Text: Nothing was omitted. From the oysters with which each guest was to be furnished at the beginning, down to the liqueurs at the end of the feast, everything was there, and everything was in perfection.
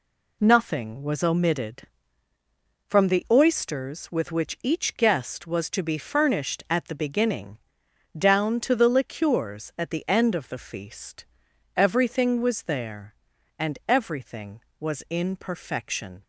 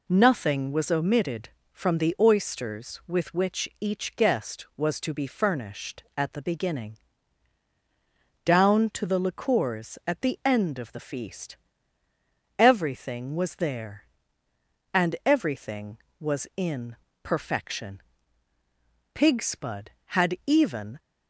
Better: first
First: none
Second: pauses between "in" and "perfection"; slight; at 16.9 s; 0.28 s long // goes on to say "Pigspud had even"; strong; from 19.1 s on; 1.8 s long

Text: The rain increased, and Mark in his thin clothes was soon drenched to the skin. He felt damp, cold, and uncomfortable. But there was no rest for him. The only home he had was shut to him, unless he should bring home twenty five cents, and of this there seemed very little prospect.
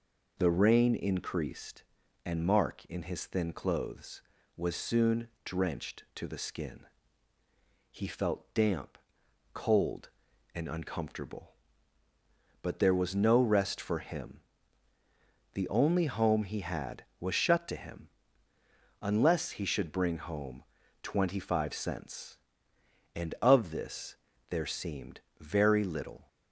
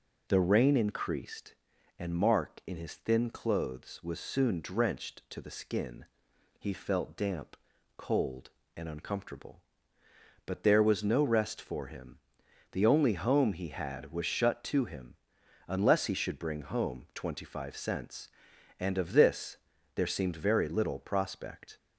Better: second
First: pauses between "home" and "twenty"; at 20.6 s; 0.38 s long // pauses between "this" and "there"; slight; at 24.1 s; 0.34 s long // pauses between "seemed" and "very"; slight; at 25.1 s; 0.20 s long // stops before "prospect"; at 26.2 s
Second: pauses between "this" and "there"; slight; at 19.5 s; 0.36 s long

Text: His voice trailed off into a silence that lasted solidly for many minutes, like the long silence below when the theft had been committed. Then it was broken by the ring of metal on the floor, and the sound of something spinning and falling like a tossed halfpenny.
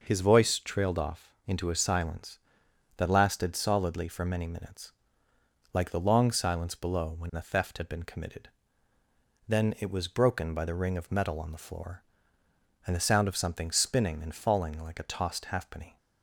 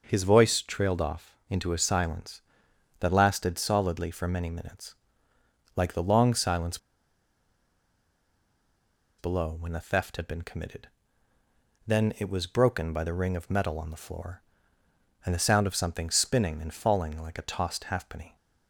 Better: first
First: none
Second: pauses between "silence" and "below"; strong; at 6.7 s; 2.4 s long

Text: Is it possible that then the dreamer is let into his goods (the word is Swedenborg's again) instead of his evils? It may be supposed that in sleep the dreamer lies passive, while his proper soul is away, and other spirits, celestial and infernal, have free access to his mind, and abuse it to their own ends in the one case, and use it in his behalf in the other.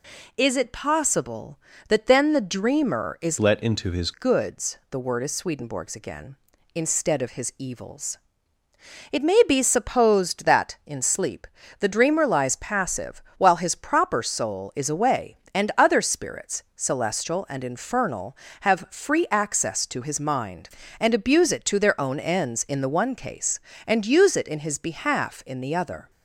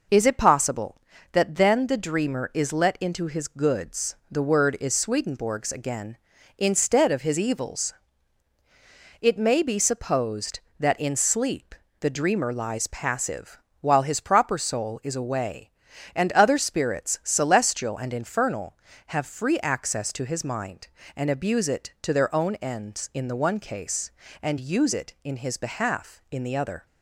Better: second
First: changes voice from "let" to "his"; from 3.3 to 4.1 s; 0.8 s long // pauses between "sleep" and "the"; slight; at 11.4 s; 0.32 s long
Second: pauses between "sleep" and "the"; slight; at 11.7 s; 0.26 s long

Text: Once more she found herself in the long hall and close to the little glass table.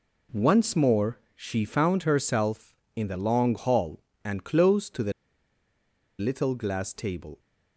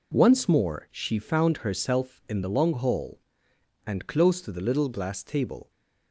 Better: second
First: pauses between "more" and "she"; slight; at 1.1 s; 0.16 s long // pauses between "the" and "little"; at 5.1 s; 1.0 s long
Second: none

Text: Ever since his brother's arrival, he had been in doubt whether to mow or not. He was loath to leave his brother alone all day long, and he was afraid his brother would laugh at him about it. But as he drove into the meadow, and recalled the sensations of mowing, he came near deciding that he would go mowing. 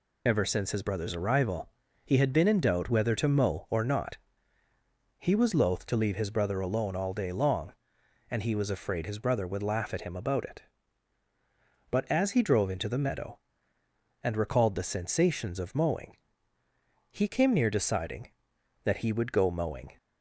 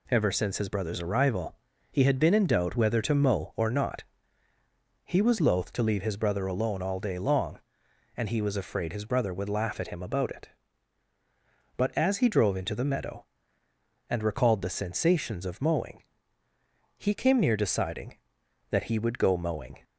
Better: second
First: loses the start of "Ever"; at 0.2 s; 55 ms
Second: none

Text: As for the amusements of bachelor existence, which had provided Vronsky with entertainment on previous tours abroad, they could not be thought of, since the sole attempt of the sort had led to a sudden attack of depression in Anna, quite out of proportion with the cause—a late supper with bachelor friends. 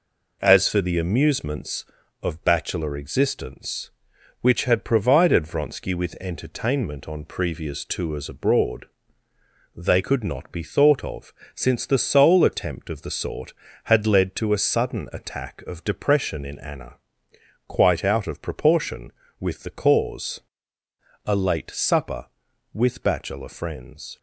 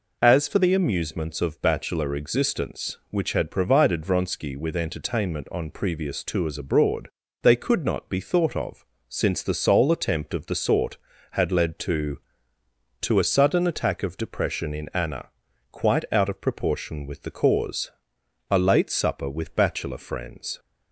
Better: first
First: none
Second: says "to" twice; at 12.9 s

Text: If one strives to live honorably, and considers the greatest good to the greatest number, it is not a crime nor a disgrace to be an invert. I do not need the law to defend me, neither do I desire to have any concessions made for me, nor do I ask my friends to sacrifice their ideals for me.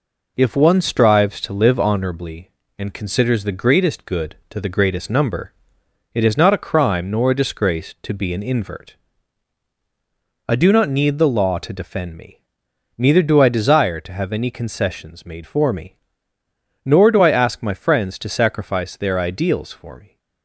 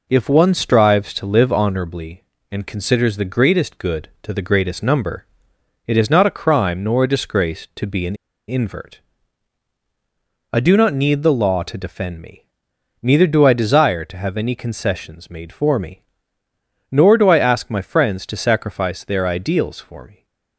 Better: first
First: none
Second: pauses between "an" and "invert"; slight; at 8.1 s; 0.32 s long

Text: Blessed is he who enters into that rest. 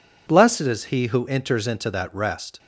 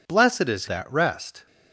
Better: first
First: none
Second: skips "he who enters into"; at 0.6 s

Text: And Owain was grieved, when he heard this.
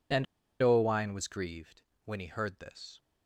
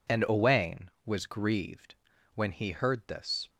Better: second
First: pauses between "And" and "Owain"; at 0.2 s; 0.37 s long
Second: none

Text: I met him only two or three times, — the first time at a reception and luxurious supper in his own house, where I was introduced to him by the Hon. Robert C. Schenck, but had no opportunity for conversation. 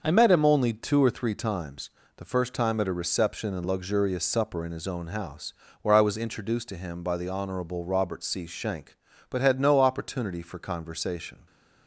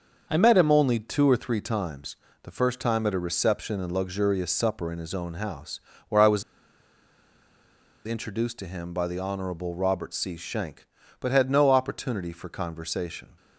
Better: first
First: starts louder than the rest; until 1.0 s; 6.5 dB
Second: starts louder than the rest; until 1.3 s; 6.5 dB // pauses between "was" and "introduced"; strong; at 6.4 s; 1.6 s long

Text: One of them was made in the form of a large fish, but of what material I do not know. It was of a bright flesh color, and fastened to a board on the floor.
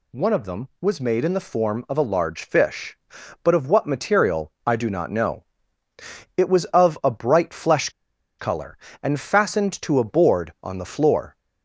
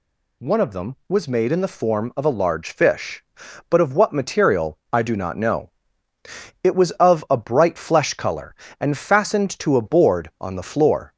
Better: second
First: pauses between "flesh" and "color"; noticeable; at 7.8 s; 0.49 s long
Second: none

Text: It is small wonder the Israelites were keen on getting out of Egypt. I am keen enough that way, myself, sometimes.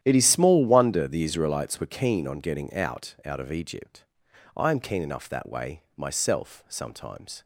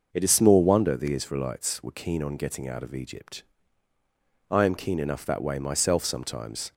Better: second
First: starts louder than the rest; strong; until 1.0 s; 11 dB // says "out" twice; at 3.2 s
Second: none

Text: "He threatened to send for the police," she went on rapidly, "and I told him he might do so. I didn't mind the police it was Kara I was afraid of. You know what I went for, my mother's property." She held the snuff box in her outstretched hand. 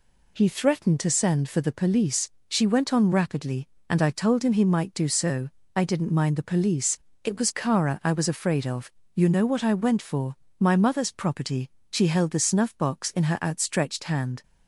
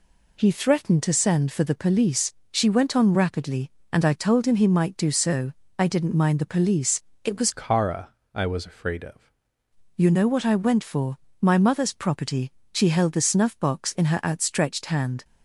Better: first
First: pauses between "police" and "it"; slight; at 6.9 s; 0.24 s long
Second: pauses between "police" and "it"; slight; at 7.0 s; 0.22 s long // changes voice from "Kara" to "of"; from 7.5 to 9.3 s; 1.8 s long // pauses between "Kara" and "I"; slight; at 8.1 s; 0.20 s long

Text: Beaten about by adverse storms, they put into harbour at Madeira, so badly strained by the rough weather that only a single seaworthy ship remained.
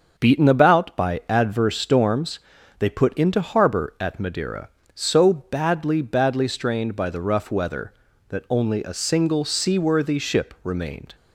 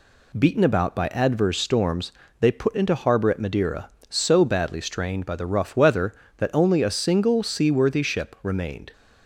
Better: second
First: starts louder than the rest; until 1.2 s; 6.5 dB // says "badly" twice; at 6.0 s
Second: none

